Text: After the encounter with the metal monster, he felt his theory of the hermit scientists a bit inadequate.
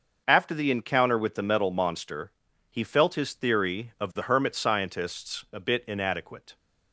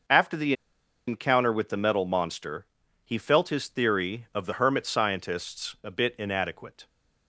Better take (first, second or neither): first